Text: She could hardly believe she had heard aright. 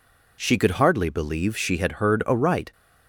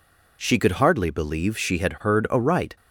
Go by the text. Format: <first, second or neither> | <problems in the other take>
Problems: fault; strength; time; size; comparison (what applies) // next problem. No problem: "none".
neither | none